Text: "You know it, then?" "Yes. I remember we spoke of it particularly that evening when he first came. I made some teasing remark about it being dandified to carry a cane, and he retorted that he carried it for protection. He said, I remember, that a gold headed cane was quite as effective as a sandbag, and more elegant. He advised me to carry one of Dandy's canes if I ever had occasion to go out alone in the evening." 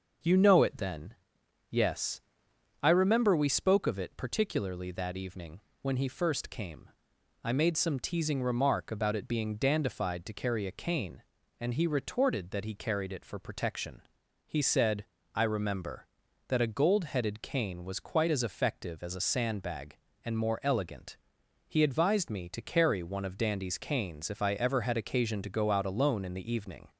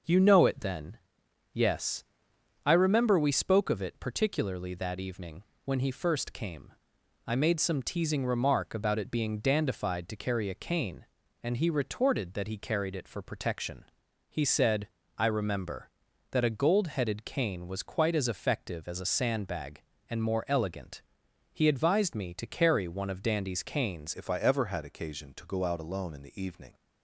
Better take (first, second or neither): first